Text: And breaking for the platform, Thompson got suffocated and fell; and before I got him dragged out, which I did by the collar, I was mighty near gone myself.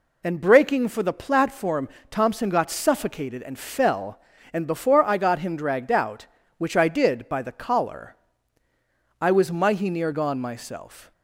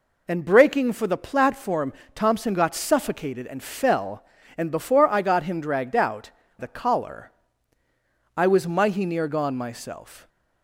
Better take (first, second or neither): first